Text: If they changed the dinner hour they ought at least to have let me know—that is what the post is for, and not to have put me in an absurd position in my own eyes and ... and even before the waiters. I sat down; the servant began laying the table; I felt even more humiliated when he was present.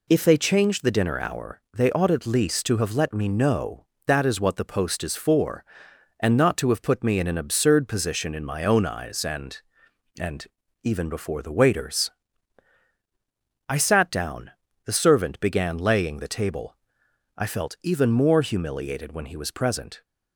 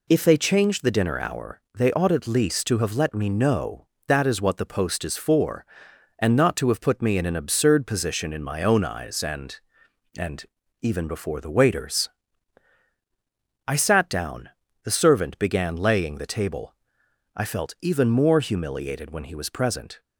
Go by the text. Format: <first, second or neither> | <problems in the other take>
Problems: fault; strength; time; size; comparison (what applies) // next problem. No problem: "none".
neither | pauses between "and" and "even"; slight; the same in both